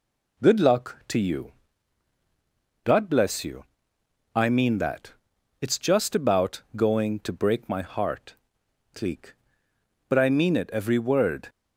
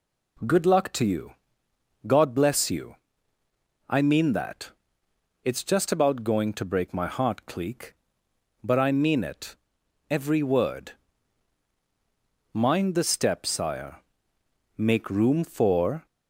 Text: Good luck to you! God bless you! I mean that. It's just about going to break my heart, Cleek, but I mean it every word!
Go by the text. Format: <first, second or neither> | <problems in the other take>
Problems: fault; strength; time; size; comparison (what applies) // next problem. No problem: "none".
first | pauses between "it" and "every"; noticeable; at 9.5 s; 0.56 s long // goes on to say "Mind the step Sire Make room for"; strong; from 12.5 s on; 3.5 s long